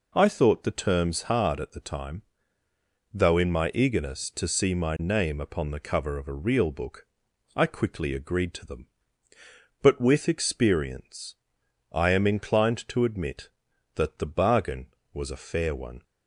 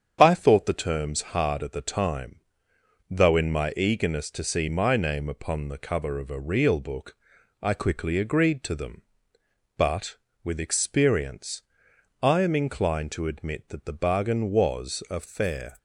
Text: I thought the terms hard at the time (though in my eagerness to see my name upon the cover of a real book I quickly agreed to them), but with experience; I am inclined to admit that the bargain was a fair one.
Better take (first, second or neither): first